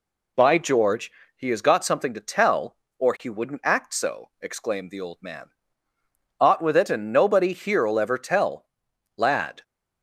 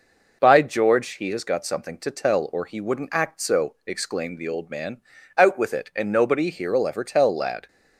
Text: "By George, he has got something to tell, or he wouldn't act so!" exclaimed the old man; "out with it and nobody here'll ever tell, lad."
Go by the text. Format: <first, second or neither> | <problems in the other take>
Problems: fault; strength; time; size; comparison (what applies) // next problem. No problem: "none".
second | says "ought" for "out"; at 6.3 s